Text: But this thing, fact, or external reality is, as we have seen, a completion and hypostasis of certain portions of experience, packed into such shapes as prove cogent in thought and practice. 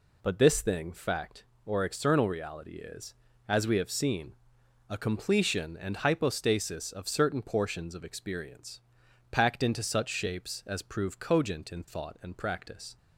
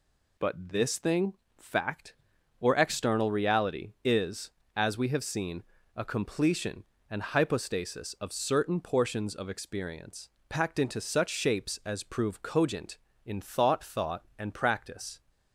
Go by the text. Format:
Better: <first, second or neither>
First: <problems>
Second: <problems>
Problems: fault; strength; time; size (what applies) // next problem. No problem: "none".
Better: first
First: none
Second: says "thought" twice; at 13.8 s